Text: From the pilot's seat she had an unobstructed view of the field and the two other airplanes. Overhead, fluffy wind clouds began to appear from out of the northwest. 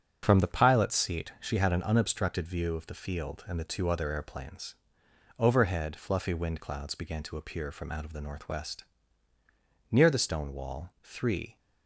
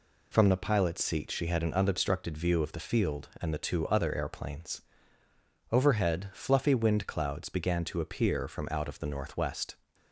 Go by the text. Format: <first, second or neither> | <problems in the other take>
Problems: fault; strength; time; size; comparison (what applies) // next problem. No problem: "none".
second | starts louder than the rest; strong; until 1.2 s; 7.5 dB // goes on to say "Near the stone wall three"; from 9.9 s on; 1.6 s long